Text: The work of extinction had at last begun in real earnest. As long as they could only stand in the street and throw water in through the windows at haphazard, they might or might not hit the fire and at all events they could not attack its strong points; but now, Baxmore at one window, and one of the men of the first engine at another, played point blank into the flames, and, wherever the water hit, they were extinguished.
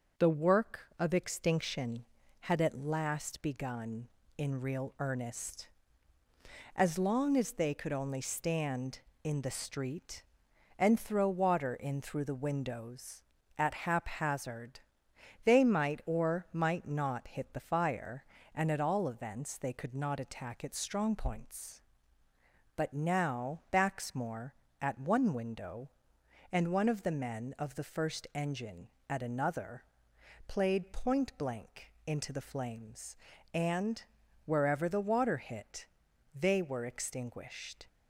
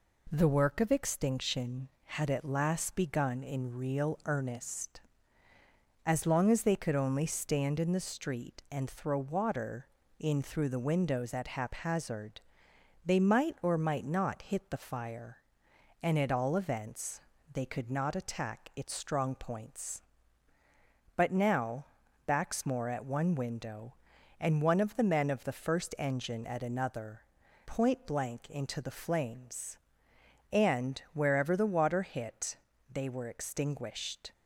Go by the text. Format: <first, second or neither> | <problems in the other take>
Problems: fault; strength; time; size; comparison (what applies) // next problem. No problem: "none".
first | pauses between "events" and "they"; slight; at 17.2 s; 0.32 s long // skips "played"; at 27.4 s